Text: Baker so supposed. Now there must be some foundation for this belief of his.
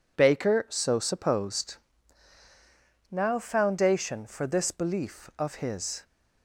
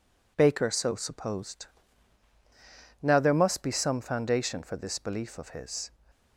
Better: second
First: skips "there must be some"; at 3.3 s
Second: none

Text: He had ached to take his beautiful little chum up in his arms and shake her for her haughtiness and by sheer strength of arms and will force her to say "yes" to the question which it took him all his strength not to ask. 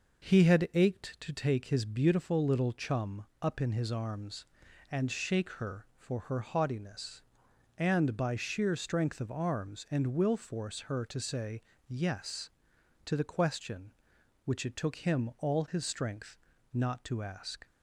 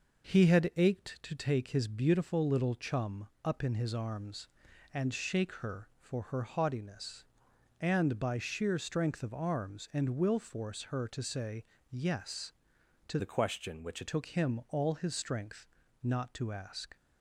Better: first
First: pauses between "chum" and "up"; slight; at 3.2 s; 0.16 s long // pauses between "say" and "yes"; slight; at 11.6 s; 0.28 s long // pauses between "strength" and "not"; slight; at 16.3 s; 0.34 s long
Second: pauses between "chum" and "up"; slight; at 3.2 s; 0.16 s long // pauses between "say" and "yes"; slight; at 11.6 s; 0.28 s long // changes voice from "the" to "it"; from 13.1 to 14.0 s; 0.9 s long // pauses between "strength" and "not"; slight; at 15.6 s; 0.34 s long

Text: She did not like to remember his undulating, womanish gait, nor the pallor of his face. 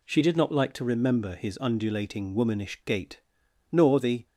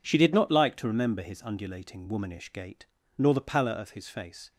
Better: second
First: stops before "pallor of his face"; at 4.2 s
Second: none

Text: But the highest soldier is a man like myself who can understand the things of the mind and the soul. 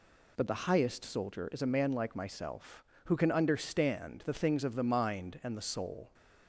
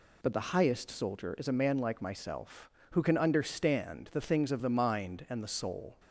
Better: neither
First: none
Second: none

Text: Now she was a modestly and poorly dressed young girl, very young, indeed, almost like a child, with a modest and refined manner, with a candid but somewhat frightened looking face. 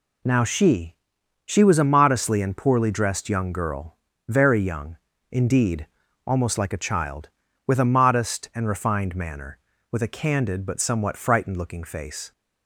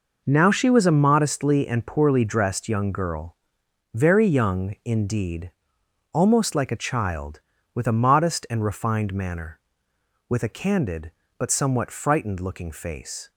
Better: second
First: says "she" twice; at 1.4 s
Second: none

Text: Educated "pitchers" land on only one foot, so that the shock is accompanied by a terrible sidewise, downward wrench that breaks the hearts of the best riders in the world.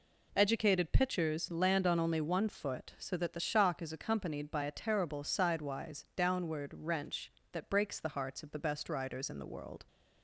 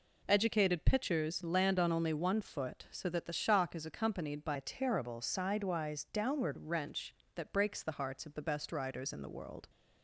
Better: first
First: none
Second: changes voice from "a" to "downward"; from 4.5 to 6.5 s; 2.0 s long

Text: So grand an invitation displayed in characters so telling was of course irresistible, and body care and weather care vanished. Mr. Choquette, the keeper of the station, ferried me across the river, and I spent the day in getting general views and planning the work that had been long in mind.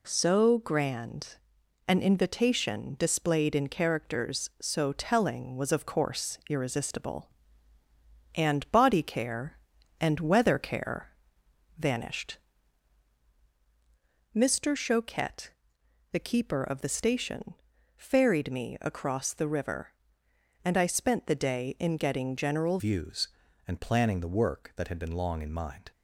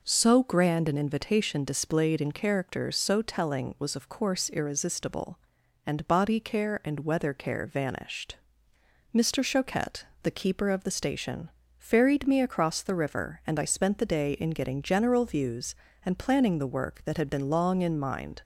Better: second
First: pauses between "grand" and "an"; noticeable; at 1.3 s; 0.50 s long // pauses between "care" and "vanished"; noticeable; at 11.0 s; 0.70 s long // changes voice at "views"; from 22.7 s on; 3.2 s long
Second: none

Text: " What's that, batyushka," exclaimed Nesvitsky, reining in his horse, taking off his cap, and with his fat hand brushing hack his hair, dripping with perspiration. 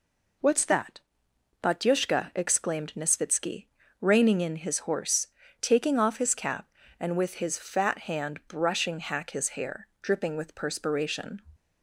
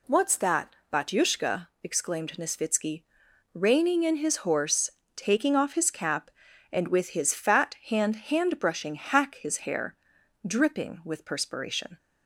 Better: first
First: none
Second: says "hand" twice; at 8.1 s

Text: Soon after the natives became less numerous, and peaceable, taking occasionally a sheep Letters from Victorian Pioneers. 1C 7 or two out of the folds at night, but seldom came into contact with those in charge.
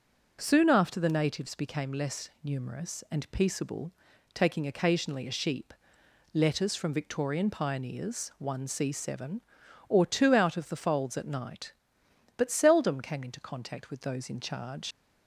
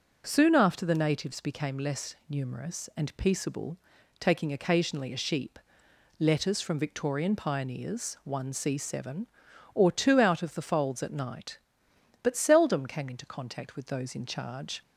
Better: second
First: pauses between "sheep" and "Letters"; noticeable; at 5.7 s; 0.60 s long // leaves "charge" unfinished; at 14.9 s; 45 ms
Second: pauses between "sheep" and "Letters"; noticeable; at 5.5 s; 0.60 s long

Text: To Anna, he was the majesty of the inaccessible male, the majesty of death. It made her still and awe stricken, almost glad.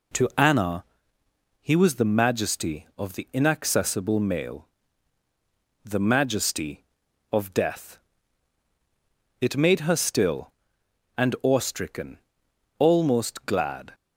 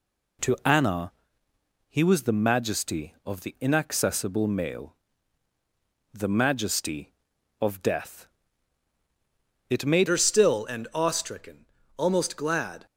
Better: first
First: none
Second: changes voice at "her"; from 10.0 s on; 2.8 s long

